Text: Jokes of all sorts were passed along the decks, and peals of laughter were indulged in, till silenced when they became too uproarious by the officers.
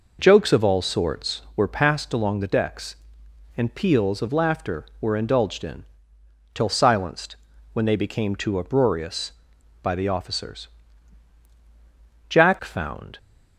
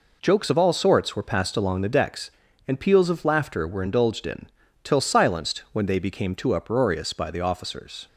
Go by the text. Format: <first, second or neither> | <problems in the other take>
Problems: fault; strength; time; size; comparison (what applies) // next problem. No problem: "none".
second | pauses between "silenced" and "when"; slight; at 7.3 s; 0.36 s long // goes on to say "Jack found"; noticeable; from 12.2 s on; 0.89 s long